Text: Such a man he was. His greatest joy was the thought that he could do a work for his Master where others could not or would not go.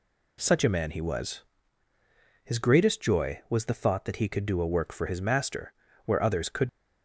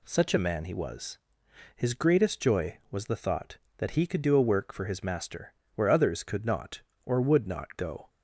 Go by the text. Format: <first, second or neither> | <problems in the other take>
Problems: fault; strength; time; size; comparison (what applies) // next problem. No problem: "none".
second | pauses between "Master" and "where"; slight; at 5.7 s; 0.32 s long; slight in the second // stops before "not or would not go"; at 6.6 s